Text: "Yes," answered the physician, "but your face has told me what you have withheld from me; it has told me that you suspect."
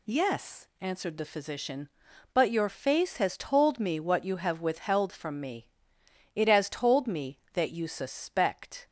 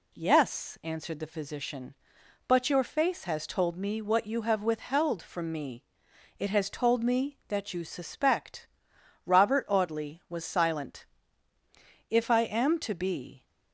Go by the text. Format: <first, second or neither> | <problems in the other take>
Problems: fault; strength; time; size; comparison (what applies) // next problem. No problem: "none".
first | goes on to say "Robert Audley was silent If I am to be"; strong; from 9.2 s on; 4.2 s long